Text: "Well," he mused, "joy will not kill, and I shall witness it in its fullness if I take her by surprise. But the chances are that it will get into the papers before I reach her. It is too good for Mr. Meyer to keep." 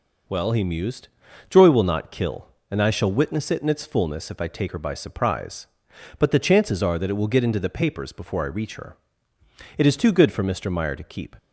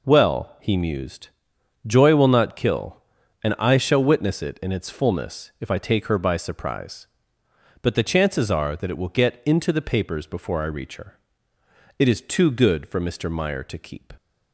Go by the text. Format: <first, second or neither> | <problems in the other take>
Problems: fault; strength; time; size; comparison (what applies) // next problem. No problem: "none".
neither | none